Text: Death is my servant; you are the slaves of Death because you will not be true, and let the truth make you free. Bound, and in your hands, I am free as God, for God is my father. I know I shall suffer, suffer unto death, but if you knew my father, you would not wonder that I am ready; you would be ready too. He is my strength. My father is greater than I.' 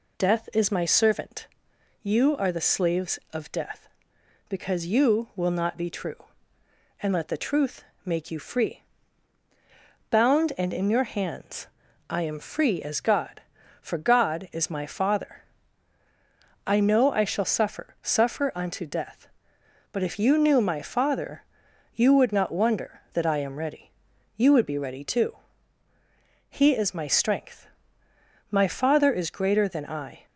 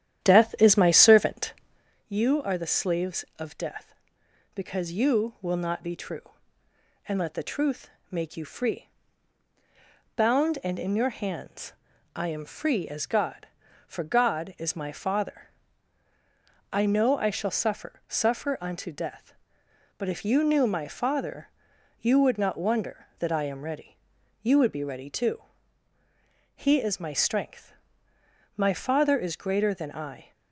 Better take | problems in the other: first | starts louder than the rest; strong; until 2.0 s; 10.5 dB // pauses between "truth" and "make"; slight; at 7.8 s; 0.22 s long; slight in the first

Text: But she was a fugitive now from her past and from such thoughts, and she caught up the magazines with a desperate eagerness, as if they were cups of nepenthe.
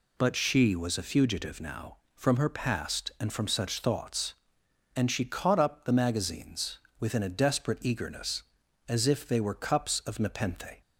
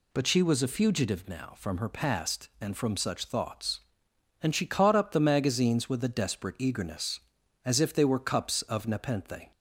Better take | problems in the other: second | says "within" for "with"; at 6.9 s

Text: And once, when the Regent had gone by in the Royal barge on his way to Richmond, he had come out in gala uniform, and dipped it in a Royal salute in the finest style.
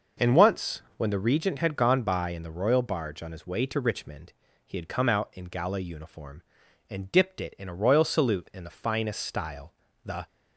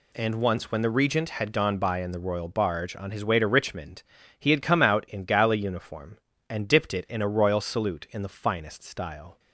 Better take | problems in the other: second | goes on to say "The"; slight; from 10.0 s on; 0.22 s long

